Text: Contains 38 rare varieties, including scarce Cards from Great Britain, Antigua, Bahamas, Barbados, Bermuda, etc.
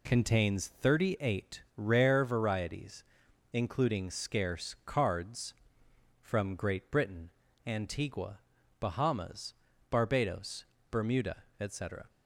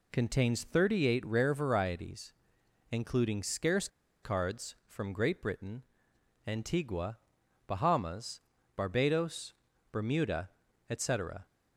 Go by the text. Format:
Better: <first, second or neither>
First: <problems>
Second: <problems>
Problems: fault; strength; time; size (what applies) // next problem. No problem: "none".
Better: first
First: none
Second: pauses between "scarce" and "Cards"; slight; at 3.8 s; 0.35 s long